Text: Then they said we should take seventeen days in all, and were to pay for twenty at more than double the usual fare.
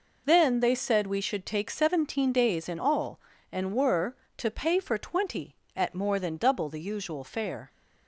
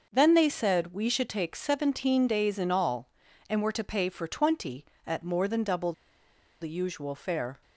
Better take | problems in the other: first | pauses between "double" and "the"; noticeable; at 5.9 s; 0.69 s long

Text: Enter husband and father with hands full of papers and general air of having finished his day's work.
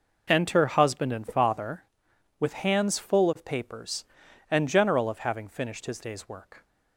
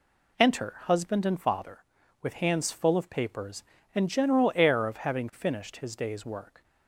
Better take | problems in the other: second | skips "air"; at 5.0 s

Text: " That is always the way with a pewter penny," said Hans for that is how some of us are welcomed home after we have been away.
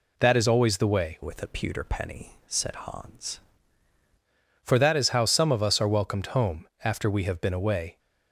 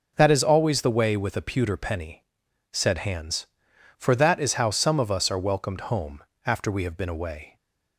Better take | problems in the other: second | changes voice from "with" to "Hans"; from 1.2 to 3.3 s; 2.1 s long // pauses between "home" and "after"; slight; at 6.6 s; 0.16 s long; slight in the second

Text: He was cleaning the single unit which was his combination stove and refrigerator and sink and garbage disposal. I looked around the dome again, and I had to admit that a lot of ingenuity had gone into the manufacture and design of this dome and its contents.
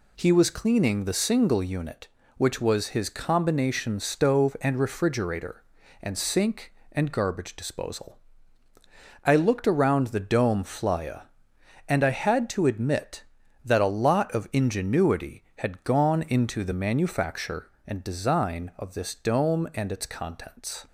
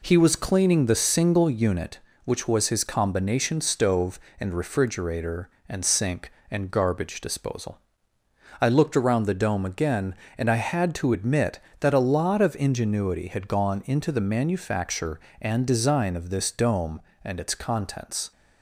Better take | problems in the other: second | says "flya" for "again"; at 10.6 s

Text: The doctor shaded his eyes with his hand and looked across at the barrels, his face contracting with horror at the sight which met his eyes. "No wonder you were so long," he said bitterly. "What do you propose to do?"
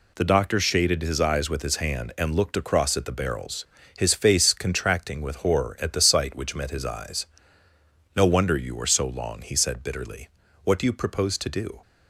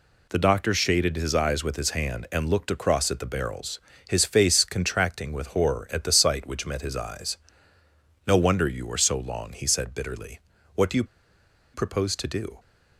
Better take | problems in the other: first | pauses between "you" and "propose"; noticeable; at 11.0 s; 0.70 s long

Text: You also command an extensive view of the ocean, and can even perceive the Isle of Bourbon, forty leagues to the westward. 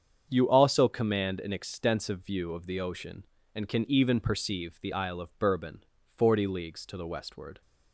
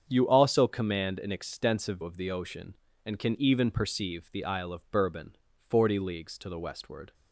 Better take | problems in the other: first | starts louder than the rest; strong; until 1.1 s; 7.5 dB; strong in the first // skips "view"; at 2.0 s

